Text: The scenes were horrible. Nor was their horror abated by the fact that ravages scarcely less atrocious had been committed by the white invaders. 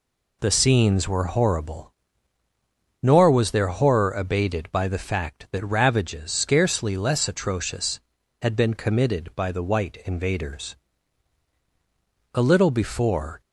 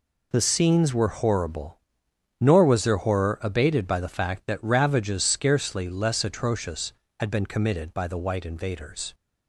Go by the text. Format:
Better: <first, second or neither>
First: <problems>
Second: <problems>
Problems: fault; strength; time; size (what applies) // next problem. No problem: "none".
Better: second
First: goes on to say "A little before"; noticeable; from 12.3 s on; 1.0 s long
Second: none